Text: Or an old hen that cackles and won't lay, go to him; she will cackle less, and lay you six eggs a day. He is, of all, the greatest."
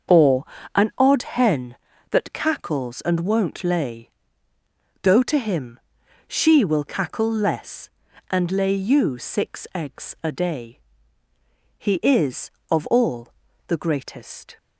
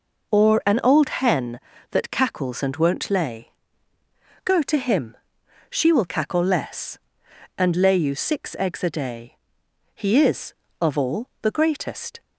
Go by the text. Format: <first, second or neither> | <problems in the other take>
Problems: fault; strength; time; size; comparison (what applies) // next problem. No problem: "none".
second | starts louder than the rest; until 1.4 s; 6.5 dB // pauses between "Or" and "an"; slight; at 0.4 s; 0.30 s long // says "odd" for "old"; at 0.9 s